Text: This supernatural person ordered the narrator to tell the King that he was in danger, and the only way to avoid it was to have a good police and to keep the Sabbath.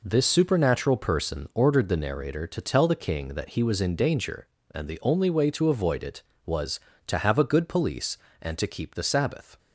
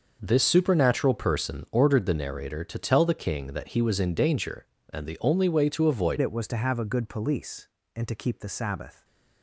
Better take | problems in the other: first | changes voice at "it"; from 6.2 s on; 2.8 s long

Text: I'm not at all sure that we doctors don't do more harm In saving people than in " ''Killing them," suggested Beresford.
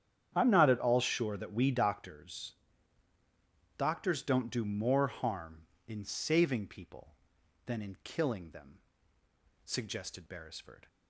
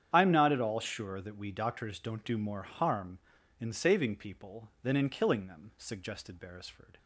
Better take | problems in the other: second | starts louder than the rest; strong; until 1.3 s; 9.5 dB; strong in the second // says "doctors" twice; at 3.7 s

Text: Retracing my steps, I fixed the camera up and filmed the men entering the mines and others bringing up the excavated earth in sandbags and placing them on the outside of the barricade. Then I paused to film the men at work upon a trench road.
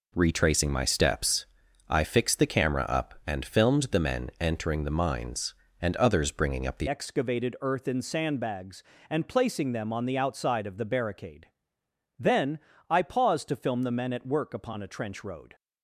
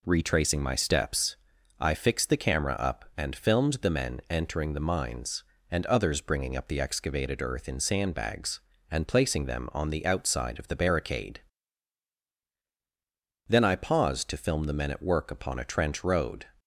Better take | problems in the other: second | changes voice at "excavated"; from 6.8 s on; 8.7 s long // pauses between "Then" and "I"; slight; at 12.5 s; 0.30 s long

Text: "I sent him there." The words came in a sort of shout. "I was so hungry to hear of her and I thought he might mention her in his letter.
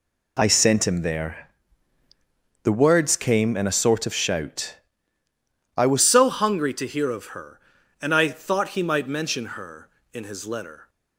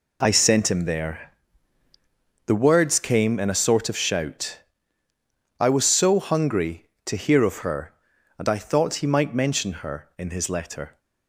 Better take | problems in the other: second | changes voice at "so"; from 6.0 s on; 4.8 s long

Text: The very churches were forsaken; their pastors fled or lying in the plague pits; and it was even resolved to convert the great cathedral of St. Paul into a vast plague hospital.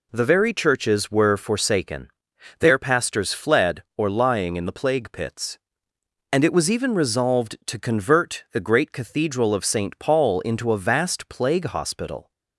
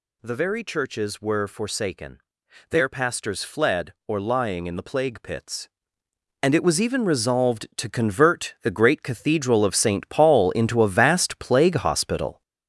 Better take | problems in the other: first | gets louder; noticeable; throughout; 6 dB

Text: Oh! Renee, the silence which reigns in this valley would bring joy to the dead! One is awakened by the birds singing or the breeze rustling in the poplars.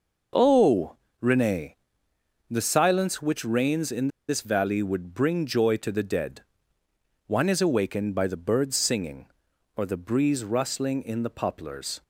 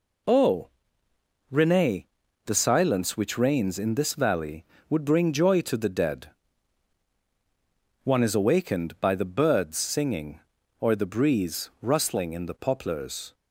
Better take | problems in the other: second | pauses between "in" and "this"; slight; at 4.0 s; 0.20 s long

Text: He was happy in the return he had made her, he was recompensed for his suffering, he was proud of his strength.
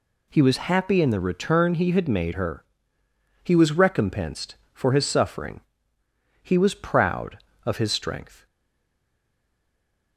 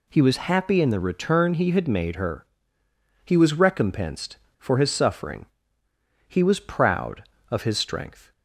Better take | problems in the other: second | stays silent after the last word; noticeable; from 8.4 s on; 1.7 s long

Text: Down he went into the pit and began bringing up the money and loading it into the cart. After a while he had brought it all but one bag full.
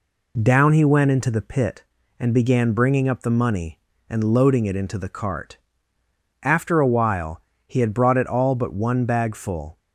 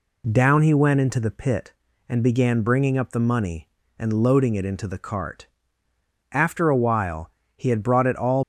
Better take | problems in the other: first | pauses between "while" and "he"; slight; at 7.2 s; 0.26 s long; slight in the first // stops before "but one bag full"; at 8.4 s

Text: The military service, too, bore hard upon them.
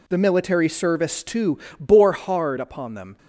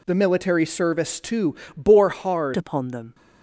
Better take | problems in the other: first | changes voice at "upon"; from 2.5 s on; 0.6 s long

